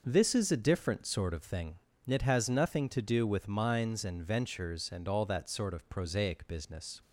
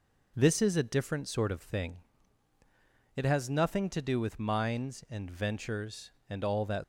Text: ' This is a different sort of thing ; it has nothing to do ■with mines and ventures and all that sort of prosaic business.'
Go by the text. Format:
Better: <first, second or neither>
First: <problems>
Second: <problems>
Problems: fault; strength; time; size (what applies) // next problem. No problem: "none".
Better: first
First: none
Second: stops before "sort of prosaic business"; at 6.8 s